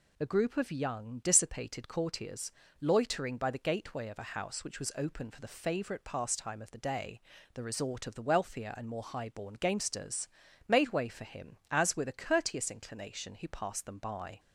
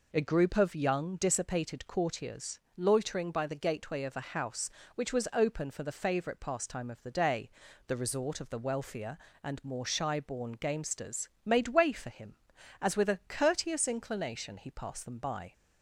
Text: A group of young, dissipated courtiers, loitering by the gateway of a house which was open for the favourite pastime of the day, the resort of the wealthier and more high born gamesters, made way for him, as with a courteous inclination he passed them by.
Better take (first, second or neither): first